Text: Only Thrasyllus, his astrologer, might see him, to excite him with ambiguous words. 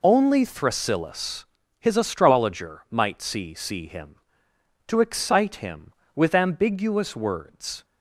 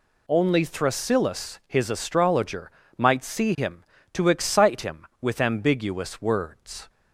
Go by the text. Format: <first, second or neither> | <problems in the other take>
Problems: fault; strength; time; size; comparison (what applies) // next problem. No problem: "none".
second | says "see" twice; at 3.5 s